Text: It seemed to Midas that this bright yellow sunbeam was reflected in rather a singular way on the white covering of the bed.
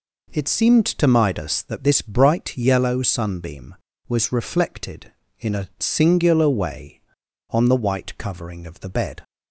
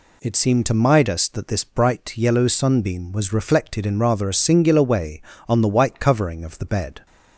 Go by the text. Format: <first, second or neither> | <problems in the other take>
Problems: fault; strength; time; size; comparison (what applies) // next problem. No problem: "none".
second | skips "rather"; at 5.5 s